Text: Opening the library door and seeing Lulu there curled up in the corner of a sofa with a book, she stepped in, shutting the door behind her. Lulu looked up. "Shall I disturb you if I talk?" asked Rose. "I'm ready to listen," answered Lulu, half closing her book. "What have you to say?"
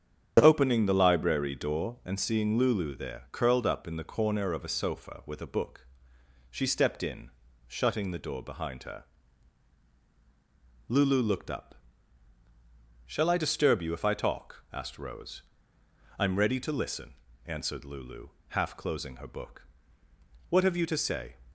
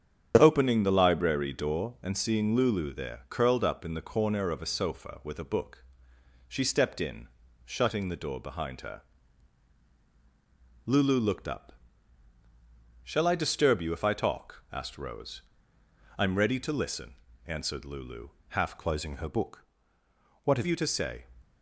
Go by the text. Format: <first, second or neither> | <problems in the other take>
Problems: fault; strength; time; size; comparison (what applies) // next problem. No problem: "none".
first | starts louder than the rest; strong; until 1.4 s; 8 dB; strong in the first // changes voice from "closing" to "have"; from 18.7 to 20.6 s; 1.9 s long